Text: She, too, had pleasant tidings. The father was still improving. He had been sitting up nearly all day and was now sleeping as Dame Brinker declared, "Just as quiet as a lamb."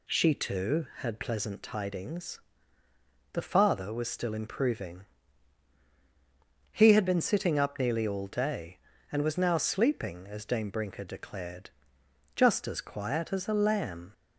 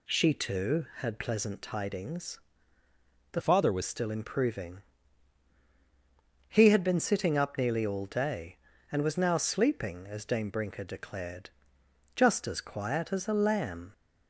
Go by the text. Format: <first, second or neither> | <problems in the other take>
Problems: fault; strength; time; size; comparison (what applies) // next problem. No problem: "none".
first | changes voice from "father" to "was"; from 3.4 to 3.8 s; 0.4 s long